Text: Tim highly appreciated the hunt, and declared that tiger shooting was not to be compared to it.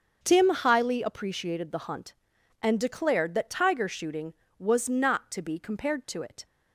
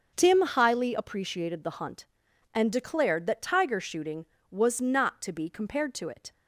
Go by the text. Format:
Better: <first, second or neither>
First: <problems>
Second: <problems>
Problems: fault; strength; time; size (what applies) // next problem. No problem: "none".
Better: neither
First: starts louder than the rest; until 1.2 s; 6.5 dB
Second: starts louder than the rest; until 1.1 s; 6.5 dB